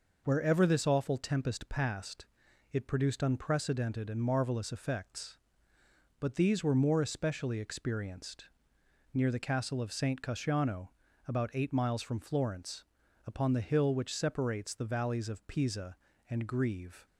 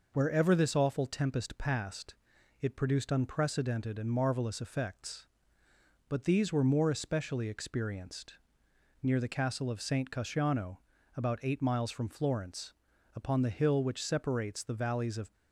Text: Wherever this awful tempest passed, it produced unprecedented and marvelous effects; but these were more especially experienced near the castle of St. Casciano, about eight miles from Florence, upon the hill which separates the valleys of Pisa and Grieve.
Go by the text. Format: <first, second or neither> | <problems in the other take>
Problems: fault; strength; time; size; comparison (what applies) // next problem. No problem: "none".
first | pauses between "experienced" and "near"; noticeable; at 8.3 s; 0.68 s long; noticeable in the first // stops before "Pisa and Grieve"; at 15.3 s